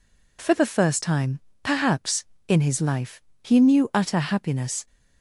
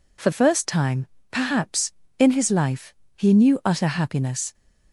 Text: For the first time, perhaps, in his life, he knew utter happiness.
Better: first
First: none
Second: skips "the"; at 0.3 s

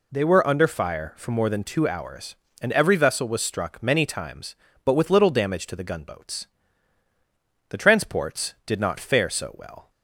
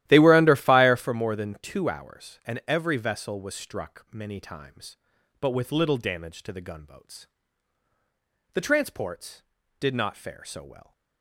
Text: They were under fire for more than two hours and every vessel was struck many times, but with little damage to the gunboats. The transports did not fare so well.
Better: first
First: none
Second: starts louder than the rest; strong; until 1.1 s; 13.5 dB

